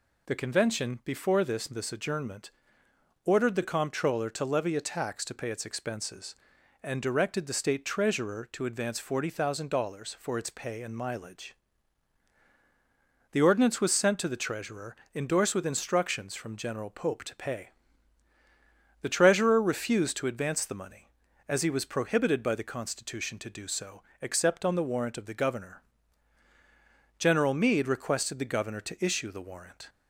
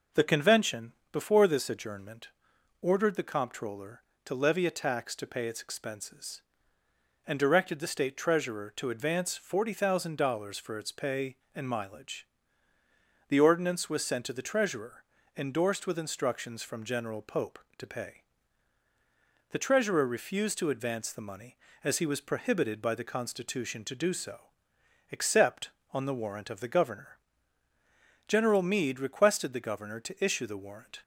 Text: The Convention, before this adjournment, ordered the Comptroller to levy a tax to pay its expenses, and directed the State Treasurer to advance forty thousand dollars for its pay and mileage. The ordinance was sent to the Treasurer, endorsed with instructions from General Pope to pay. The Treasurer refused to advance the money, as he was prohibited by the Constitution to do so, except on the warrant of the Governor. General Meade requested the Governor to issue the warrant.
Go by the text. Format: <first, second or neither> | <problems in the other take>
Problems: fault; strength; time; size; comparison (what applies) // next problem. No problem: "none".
second | says "this" twice; at 1.6 s